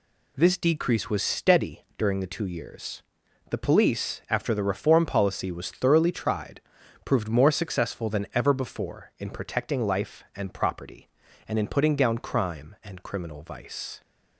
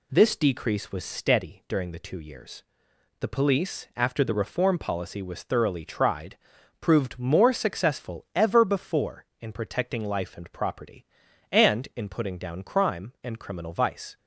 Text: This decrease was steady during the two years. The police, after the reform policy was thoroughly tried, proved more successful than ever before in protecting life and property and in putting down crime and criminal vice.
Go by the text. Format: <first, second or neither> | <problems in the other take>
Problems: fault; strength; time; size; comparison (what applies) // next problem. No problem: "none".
first | skips "than"; at 8.2 s